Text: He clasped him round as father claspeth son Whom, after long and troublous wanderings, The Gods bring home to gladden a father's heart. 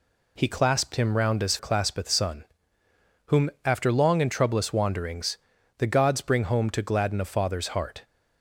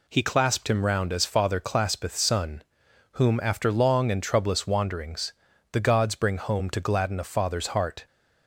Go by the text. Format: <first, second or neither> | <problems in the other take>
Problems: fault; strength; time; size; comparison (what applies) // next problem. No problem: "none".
second | skips "father"; at 1.5 s // pauses between "son" and "Whom"; noticeable; at 2.4 s; 0.84 s long; noticeable in the second